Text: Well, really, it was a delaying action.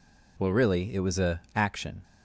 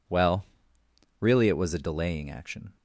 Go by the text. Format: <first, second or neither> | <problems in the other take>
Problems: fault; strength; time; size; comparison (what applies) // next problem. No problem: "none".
second | skips "delaying"; at 1.4 s